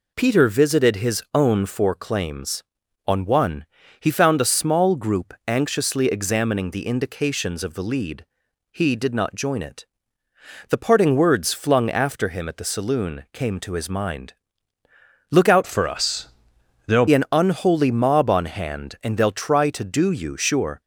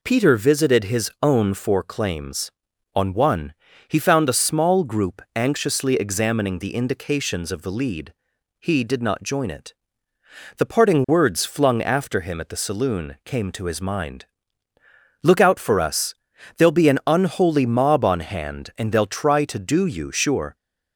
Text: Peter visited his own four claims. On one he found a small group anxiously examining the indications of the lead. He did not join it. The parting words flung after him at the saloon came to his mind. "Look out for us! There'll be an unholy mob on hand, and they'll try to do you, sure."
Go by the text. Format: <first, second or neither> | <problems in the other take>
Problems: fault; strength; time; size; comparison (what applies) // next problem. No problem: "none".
second | pauses between "one" and "he"; slight; at 3.6 s; 0.34 s long; slight in the second // changes voice from "for" to "There'll"; from 15.6 to 17.0 s; 1.4 s long